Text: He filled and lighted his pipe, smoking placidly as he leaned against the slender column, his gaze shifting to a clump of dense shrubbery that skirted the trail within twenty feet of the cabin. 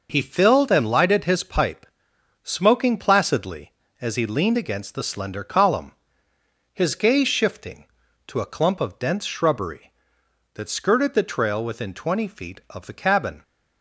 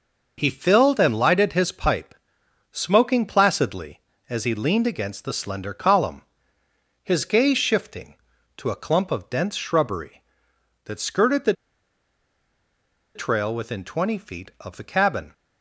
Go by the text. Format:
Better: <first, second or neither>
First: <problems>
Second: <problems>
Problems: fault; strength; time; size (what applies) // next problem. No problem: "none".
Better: first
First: none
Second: pauses between "the" and "trail"; strong; at 11.5 s; 1.6 s long